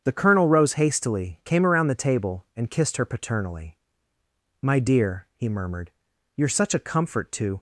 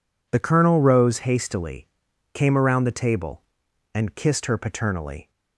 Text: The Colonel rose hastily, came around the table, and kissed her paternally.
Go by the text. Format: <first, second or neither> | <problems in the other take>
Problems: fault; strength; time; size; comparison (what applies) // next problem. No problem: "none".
second | starts louder than the rest; strong; until 1.0 s; 8 dB // goes on to say "My dear he murmured you're such a comfort to"; strong; from 4.6 s on; 2.9 s long